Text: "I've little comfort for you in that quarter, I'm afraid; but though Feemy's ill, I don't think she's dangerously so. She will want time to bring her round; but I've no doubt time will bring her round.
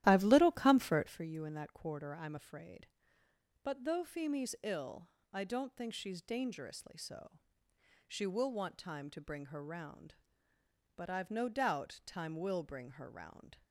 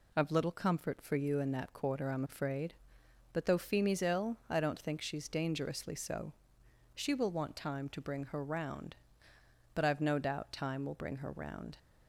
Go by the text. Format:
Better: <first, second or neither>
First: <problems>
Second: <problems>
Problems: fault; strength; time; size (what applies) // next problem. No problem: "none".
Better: second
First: starts louder than the rest; strong; until 1.2 s; 13.5 dB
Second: none